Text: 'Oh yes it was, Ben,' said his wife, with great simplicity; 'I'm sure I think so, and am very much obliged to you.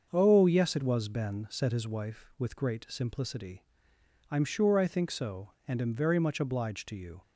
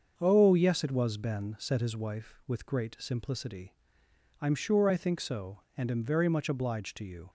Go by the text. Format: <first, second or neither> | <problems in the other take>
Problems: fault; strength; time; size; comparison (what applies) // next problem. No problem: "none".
neither | starts louder than the rest; the same in both